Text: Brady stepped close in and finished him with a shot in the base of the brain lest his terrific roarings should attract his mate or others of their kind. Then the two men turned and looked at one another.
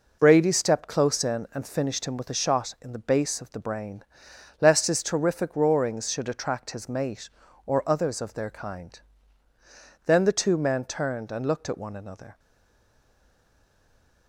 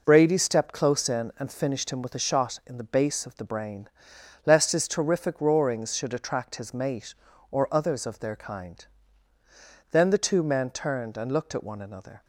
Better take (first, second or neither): second